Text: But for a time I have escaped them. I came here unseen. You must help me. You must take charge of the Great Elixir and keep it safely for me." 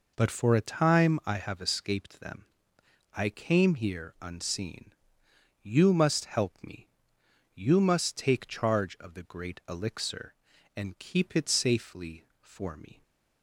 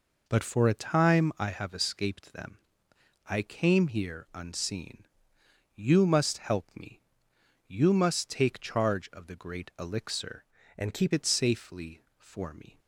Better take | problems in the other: first | changes voice from "and" to "keep"; from 10.7 to 11.1 s; 0.4 s long

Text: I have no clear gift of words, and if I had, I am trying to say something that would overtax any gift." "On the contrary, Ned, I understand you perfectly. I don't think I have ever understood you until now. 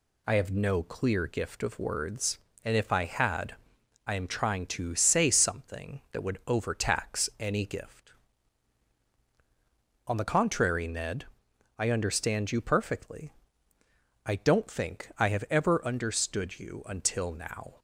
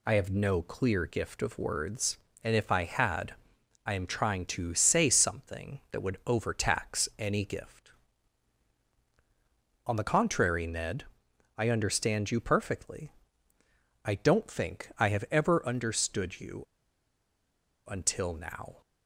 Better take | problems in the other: first | pauses between "you" and "until"; at 16.6 s; 1.2 s long

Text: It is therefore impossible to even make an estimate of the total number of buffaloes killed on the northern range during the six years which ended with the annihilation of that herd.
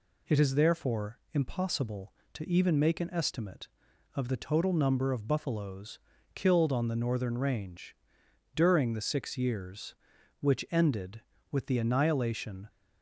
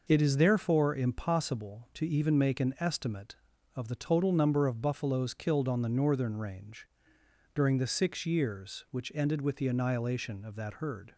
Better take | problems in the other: second | pauses between "buffaloes" and "killed"; slight; at 5.9 s; 0.36 s long // pauses between "range" and "during"; noticeable; at 7.9 s; 0.60 s long; noticeable in the second // stops before "of that herd"; at 12.6 s

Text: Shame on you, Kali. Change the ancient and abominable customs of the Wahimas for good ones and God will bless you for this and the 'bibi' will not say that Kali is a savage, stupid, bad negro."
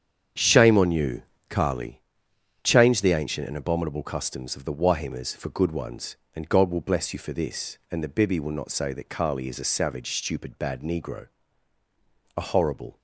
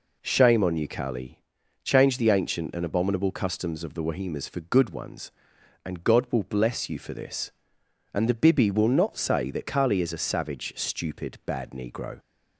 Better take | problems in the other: second | starts louder than the rest; strong; until 1.6 s; 8 dB // goes on to say "A horrible"; noticeable; from 12.3 s on; 0.62 s long

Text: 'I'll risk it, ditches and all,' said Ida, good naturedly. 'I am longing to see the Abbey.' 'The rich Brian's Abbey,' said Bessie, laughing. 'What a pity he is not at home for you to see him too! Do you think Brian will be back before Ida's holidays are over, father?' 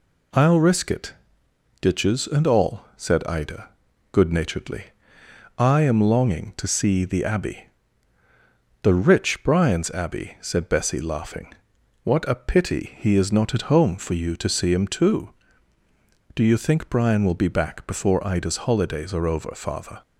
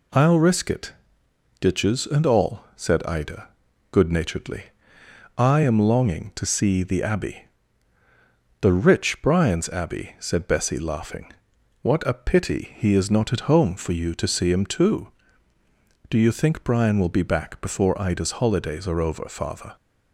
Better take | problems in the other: neither | none

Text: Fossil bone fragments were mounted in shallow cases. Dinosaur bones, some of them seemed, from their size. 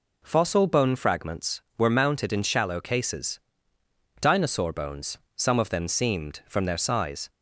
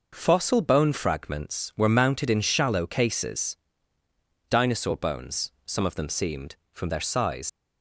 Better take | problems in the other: first | leaves "size" unfinished; at 7.4 s; 85 ms

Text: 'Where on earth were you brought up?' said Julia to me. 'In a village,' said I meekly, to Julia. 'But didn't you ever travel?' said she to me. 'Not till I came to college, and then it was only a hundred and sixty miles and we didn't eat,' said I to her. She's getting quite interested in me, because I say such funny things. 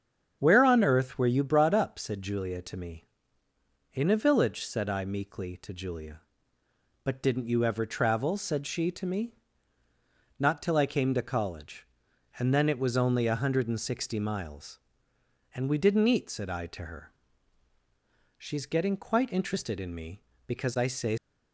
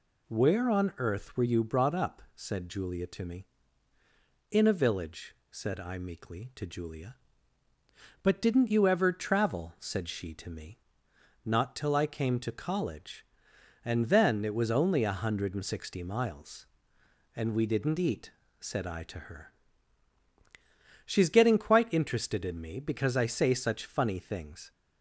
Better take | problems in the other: second | starts louder than the rest; strong; until 1.4 s; 7.5 dB // stops before "such funny things"; at 21.1 s

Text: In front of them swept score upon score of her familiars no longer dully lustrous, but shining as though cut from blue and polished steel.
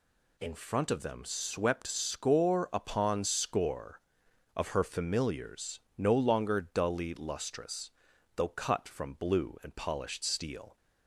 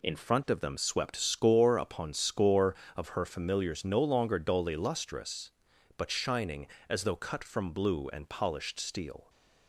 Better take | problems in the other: second | pauses between "familiars" and "no"; slight; at 5.7 s; 0.18 s long // skips "but shining as"; at 8.1 s

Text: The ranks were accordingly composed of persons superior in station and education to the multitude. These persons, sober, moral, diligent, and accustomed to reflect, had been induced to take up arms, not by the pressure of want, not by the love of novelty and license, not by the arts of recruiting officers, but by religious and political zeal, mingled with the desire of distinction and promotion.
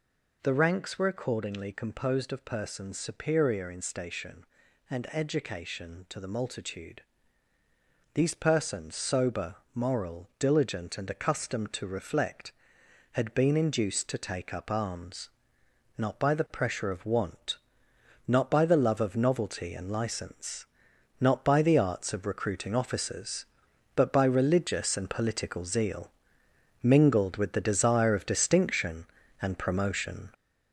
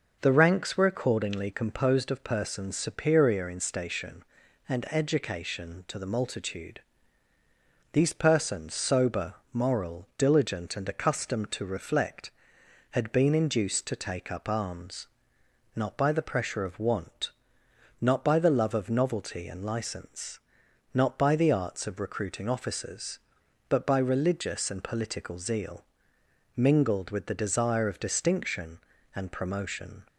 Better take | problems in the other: second | gets louder; noticeable; throughout; 5.5 dB

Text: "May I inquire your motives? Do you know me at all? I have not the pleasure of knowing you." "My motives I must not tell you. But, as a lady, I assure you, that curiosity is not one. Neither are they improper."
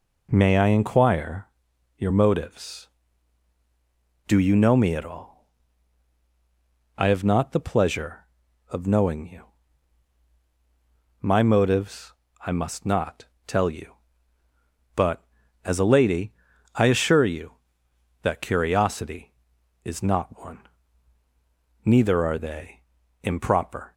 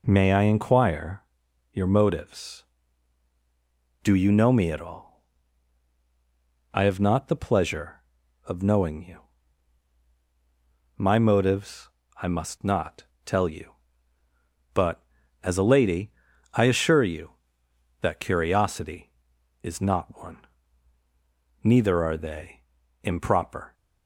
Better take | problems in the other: neither | pauses between "inquire" and "your"; noticeable; the same in both // pauses between "motives" and "I"; slight; the same in both // pauses between "not" and "tell"; slight; the same in both // pauses between "they" and "improper"; the same in both

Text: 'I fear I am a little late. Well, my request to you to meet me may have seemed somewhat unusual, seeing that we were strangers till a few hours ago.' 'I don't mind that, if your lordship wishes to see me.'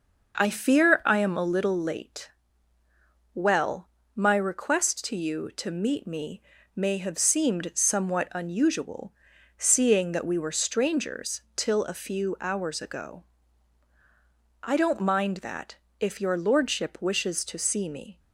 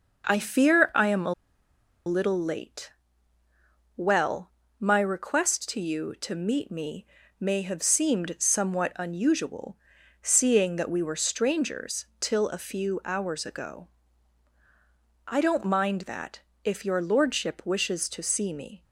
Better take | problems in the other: first | pauses between "a" and "little"; noticeable; at 1.3 s; 0.72 s long // pauses between "me" and "may"; slight; at 7.0 s; 0.34 s long; slight in the first

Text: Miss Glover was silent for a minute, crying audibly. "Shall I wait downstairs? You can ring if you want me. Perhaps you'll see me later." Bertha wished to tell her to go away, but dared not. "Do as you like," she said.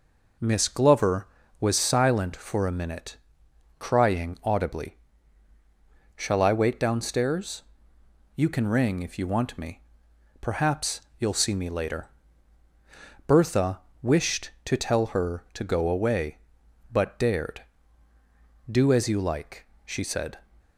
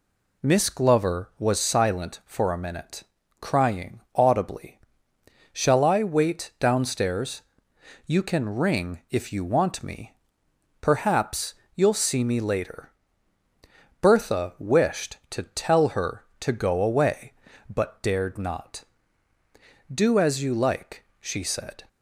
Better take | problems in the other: second | pauses between "Perhaps" and "you'll"; slight; at 11.0 s; 0.18 s long; slight in the second // pauses between "Bertha" and "wished"; slight; at 13.8 s; 0.22 s long // skips "not"; at 18.1 s

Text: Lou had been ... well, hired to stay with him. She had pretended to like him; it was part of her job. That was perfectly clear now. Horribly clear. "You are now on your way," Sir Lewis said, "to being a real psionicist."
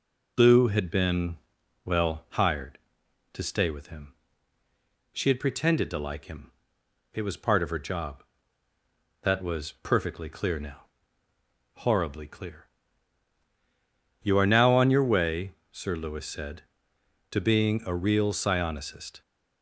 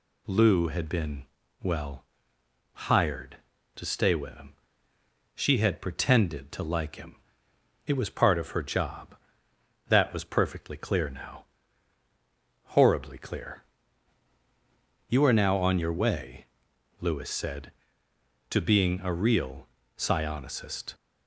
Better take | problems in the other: first | skips "Sir"; at 16.7 s // pauses between "real" and "psionicist"; slight; at 19.6 s; 0.30 s long

